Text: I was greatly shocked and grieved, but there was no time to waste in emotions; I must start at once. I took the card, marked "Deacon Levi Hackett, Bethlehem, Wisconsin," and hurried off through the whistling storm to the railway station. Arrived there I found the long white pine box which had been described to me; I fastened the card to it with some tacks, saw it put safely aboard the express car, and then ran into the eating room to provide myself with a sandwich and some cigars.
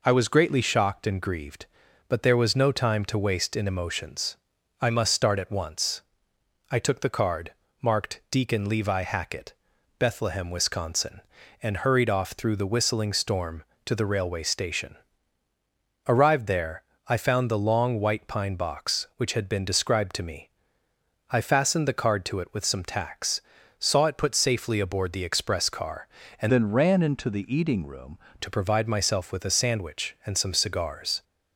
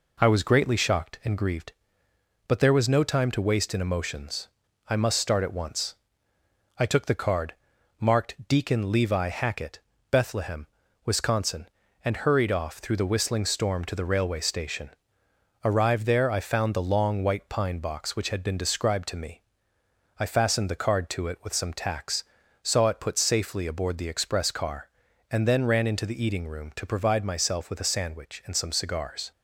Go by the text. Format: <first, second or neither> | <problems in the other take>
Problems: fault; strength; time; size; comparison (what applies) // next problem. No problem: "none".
second | pauses between "there" and "I"; slight; at 16.8 s; 0.26 s long // changes voice from "then" to "room"; from 26.4 to 28.1 s; 1.7 s long